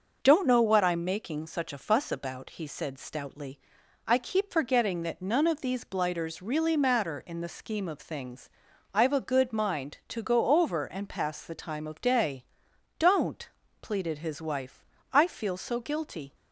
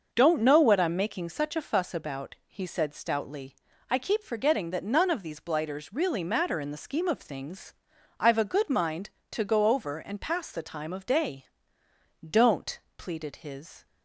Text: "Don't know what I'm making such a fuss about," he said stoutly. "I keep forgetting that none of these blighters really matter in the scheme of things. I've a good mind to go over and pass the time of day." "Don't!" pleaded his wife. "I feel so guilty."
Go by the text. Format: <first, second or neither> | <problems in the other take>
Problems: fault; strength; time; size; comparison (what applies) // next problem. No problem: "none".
first | starts louder than the rest; noticeable; until 1.1 s; 6 dB // stops before "wife I feel so guilty"; at 13.8 s